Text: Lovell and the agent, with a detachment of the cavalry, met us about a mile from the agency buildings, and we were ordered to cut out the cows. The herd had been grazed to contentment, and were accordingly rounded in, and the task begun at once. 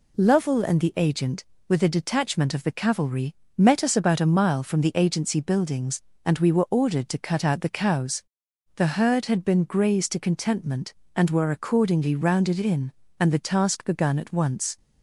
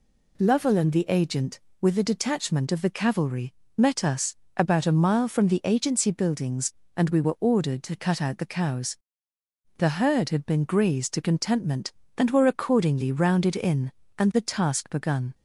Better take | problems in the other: first | pauses between "us" and "about"; slight; at 4.3 s; 0.22 s long // stops before "at once"; at 15.3 s

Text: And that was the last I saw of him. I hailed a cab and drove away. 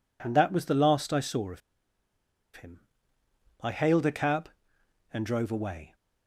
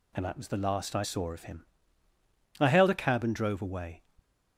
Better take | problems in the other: second | pauses between "of" and "him"; noticeable; at 1.6 s; 0.95 s long

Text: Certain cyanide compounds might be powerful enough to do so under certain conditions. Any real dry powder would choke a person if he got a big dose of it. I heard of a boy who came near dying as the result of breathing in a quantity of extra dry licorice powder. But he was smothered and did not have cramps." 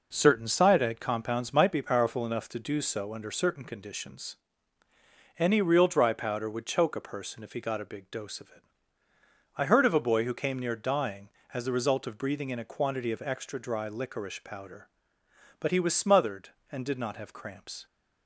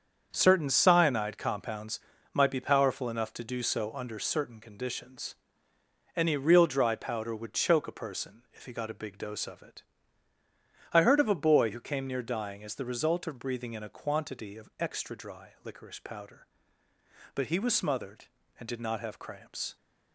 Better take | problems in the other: first | gets quieter; strong; throughout; 8.5 dB // pauses between "compounds" and "might"; slight; at 1.9 s; 0.32 s long

